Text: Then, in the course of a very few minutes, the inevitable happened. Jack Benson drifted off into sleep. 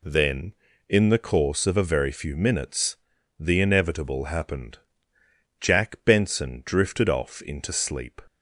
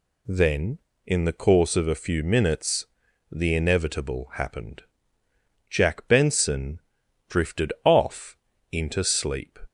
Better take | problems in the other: first | skips "very"; at 2.0 s // pauses between "Benson" and "drifted"; noticeable; at 6.8 s; 0.48 s long // pauses between "off" and "into"; slight; at 8.3 s; 0.36 s long

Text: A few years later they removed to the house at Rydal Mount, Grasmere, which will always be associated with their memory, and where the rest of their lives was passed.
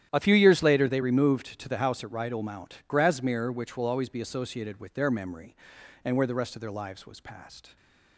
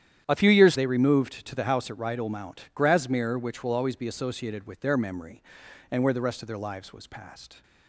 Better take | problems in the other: first | starts louder than the rest; strong; until 1.2 s; 10.5 dB; strong in the first // skips "later"; at 0.7 s

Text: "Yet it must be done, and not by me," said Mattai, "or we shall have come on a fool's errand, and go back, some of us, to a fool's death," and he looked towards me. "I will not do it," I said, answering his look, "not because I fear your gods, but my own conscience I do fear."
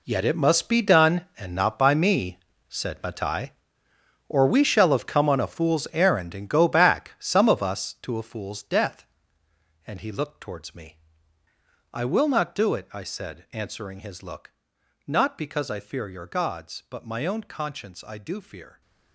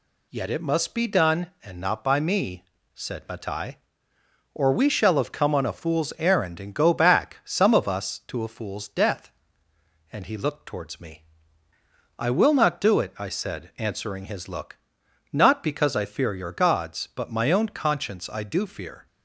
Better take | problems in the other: second | gets quieter; strong; throughout; 13.5 dB

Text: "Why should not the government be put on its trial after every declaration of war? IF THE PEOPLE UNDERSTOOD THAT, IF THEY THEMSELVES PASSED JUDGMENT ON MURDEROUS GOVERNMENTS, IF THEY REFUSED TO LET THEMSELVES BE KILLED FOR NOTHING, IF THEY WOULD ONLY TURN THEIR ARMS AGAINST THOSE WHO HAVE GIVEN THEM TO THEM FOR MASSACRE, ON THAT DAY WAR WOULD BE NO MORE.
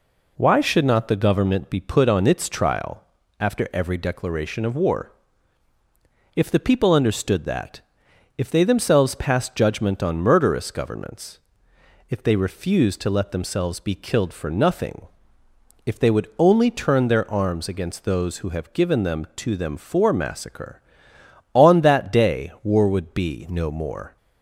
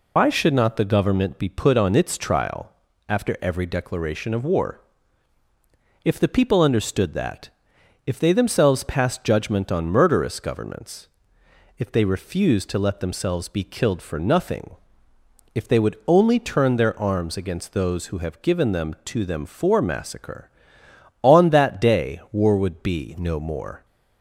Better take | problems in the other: first | loses the start of "Why"; at 0.1 s; 110 ms // pauses between "trial" and "after"; at 2.7 s; 0.38 s long; also in the first

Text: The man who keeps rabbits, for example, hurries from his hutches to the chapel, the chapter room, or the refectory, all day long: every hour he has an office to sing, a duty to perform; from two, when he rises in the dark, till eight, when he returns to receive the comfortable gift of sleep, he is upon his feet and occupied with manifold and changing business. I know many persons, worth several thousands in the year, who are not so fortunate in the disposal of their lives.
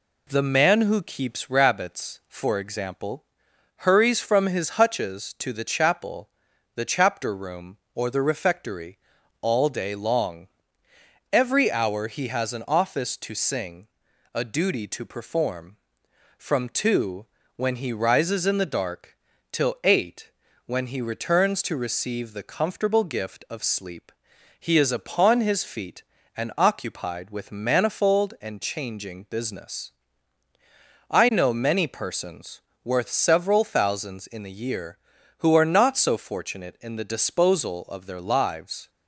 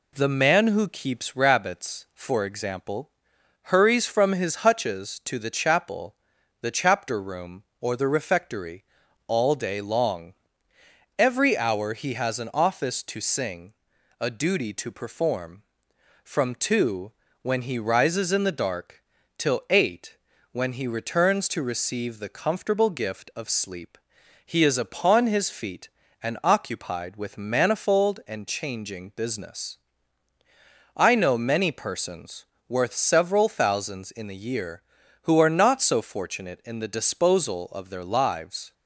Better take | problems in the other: neither | none

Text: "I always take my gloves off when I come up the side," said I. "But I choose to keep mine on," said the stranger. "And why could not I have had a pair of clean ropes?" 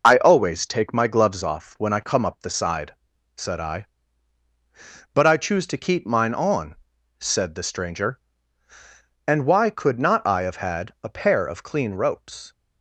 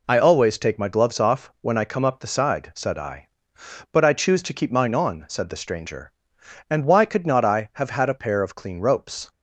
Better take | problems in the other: second | loses the start of "I"; at 0.0 s; 40 ms

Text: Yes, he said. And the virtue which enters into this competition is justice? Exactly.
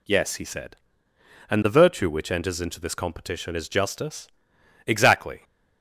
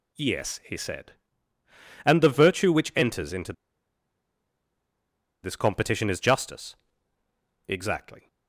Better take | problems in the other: first | pauses between "into" and "this"; strong; at 3.5 s; 1.9 s long

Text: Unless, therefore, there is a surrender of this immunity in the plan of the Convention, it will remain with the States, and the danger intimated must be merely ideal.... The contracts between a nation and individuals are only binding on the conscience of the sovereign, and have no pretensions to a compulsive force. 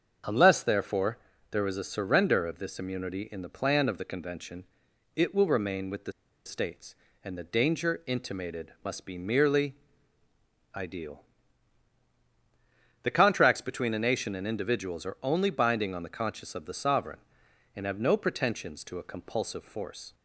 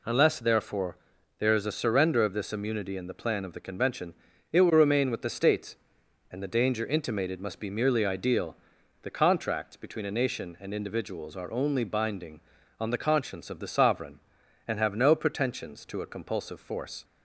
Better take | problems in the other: second | starts louder than the rest; until 1.5 s; 6.5 dB // pauses between "the" and "States"; slight; at 6.1 s; 0.33 s long // pauses between "merely" and "ideal"; at 9.7 s; 1.0 s long

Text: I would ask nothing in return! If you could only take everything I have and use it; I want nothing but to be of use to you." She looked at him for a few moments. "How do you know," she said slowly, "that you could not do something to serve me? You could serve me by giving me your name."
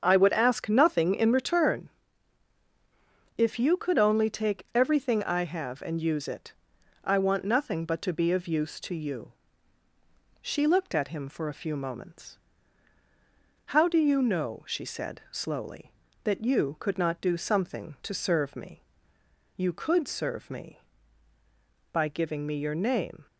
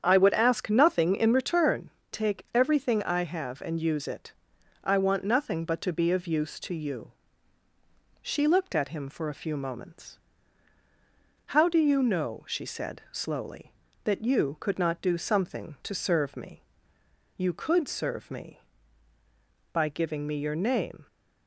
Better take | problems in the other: first | starts louder than the rest; strong; until 1.0 s; 8.5 dB; also in the first // skips "If you could only"; at 2.0 s

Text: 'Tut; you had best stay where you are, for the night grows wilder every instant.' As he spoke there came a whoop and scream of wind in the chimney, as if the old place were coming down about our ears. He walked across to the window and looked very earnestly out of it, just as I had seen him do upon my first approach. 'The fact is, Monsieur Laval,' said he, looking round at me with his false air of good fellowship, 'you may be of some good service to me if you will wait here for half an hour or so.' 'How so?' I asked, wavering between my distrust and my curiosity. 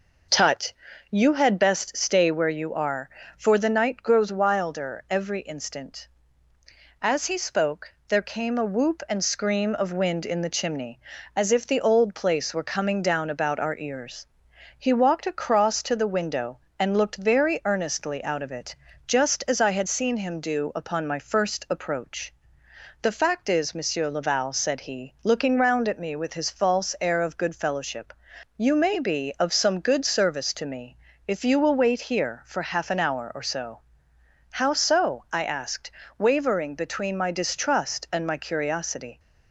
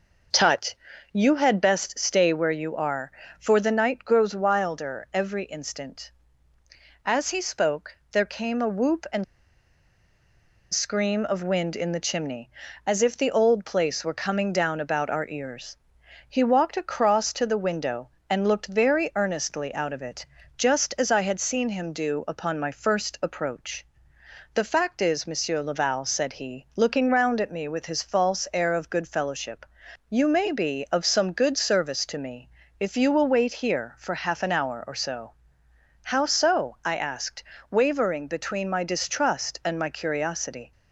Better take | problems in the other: first | pauses between "spoke" and "there"; slight; at 7.9 s; 0.16 s long; slight in the first // pauses between "and" and "scream"; strong; at 9.2 s; 1.4 s long // pauses between "me" and "if"; slight; at 32.4 s; 0.30 s long; slight in the first

